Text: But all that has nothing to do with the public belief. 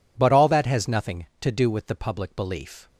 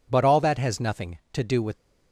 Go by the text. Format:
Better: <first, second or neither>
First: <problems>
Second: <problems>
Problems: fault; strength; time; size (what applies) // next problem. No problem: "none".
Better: first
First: none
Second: stops before "the public belief"; at 1.7 s